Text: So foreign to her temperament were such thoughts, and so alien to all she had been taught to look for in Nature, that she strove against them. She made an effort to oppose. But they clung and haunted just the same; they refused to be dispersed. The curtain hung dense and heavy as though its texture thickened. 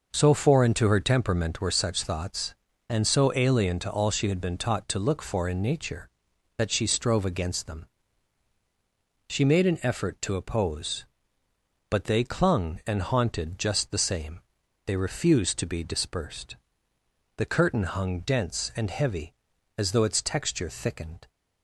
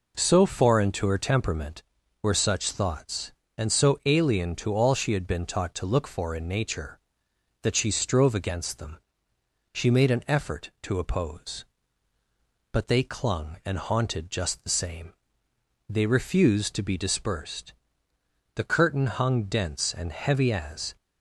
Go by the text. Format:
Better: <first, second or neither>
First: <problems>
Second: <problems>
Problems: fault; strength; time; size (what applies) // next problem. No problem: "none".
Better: first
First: none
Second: stops before "though its texture thickened"; at 20.9 s